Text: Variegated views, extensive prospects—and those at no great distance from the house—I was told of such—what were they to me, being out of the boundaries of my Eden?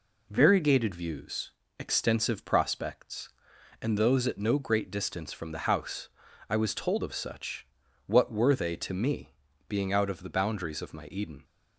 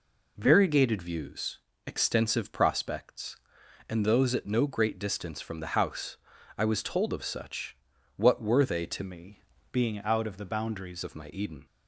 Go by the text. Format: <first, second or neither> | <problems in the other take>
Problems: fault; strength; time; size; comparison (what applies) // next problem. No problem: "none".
first | changes voice from "me" to "boundaries"; from 9.0 to 11.0 s; 2.0 s long